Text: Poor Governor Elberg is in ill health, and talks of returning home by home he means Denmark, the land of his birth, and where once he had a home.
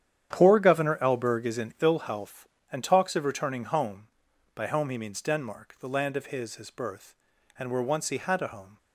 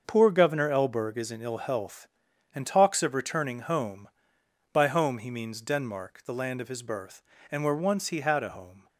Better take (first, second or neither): second